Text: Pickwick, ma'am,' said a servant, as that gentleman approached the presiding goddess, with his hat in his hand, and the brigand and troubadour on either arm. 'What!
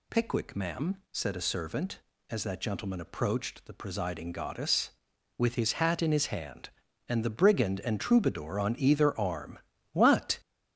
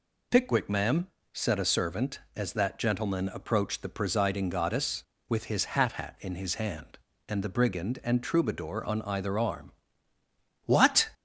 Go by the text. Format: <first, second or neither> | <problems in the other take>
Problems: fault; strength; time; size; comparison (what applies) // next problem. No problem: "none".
first | says "hat" twice; at 5.9 s